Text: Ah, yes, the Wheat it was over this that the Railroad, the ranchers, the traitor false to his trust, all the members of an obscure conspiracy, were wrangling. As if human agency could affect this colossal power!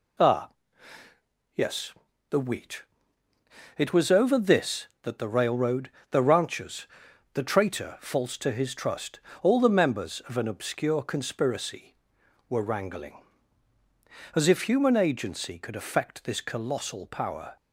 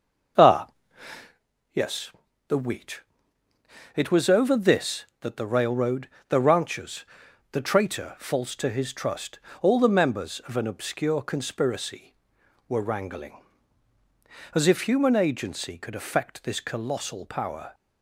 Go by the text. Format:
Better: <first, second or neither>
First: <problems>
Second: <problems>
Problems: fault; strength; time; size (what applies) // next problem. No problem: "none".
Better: first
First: pauses between "Wheat" and "it"; noticeable; at 2.8 s; 0.94 s long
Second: starts louder than the rest; until 1.3 s; 6.5 dB // pauses between "Wheat" and "it"; noticeable; at 3.0 s; 0.94 s long